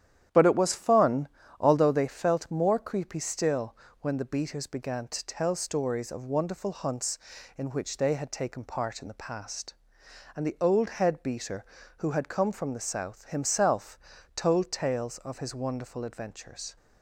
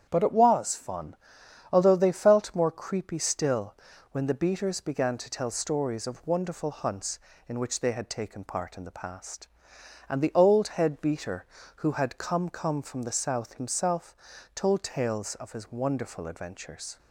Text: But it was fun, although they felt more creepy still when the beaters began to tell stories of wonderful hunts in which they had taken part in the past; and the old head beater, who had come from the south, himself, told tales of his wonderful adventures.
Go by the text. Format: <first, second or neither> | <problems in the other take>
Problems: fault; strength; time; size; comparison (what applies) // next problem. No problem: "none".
first | starts louder than the rest; strong; until 1.1 s; 9 dB; strong in the first // pauses between "still" and "when"; at 3.7 s; 0.38 s long; slight in the first // says "come" twice; at 12.4 s